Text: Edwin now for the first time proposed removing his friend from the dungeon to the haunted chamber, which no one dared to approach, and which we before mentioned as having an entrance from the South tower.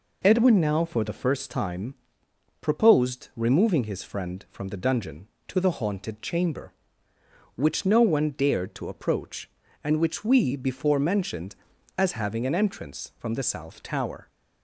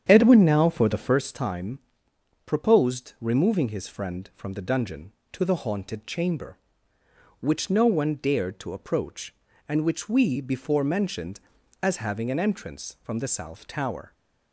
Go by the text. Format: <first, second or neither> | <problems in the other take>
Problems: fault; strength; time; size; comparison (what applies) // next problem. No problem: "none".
first | starts louder than the rest; strong; until 1.3 s; 8.5 dB // pauses between "time" and "proposed"; noticeable; at 1.7 s; 0.66 s long; noticeable in the first